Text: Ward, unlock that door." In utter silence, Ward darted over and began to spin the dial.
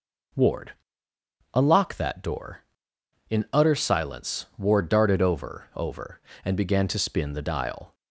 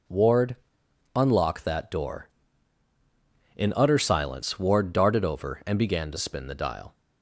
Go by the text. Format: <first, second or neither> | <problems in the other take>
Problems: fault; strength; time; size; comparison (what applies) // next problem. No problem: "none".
second | says "over" twice; at 5.7 s